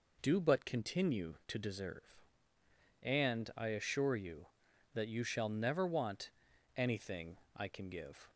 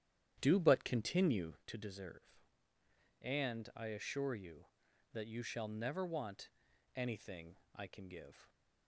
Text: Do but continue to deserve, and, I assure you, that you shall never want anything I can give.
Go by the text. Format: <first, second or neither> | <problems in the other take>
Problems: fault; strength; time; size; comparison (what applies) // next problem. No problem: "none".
first | starts louder than the rest; strong; until 1.7 s; 10.5 dB // pauses between "want" and "anything"; noticeable; at 6.4 s; 0.46 s long; noticeable in the first // pauses between "anything" and "I"; slight; at 7.5 s; 0.18 s long; slight in the first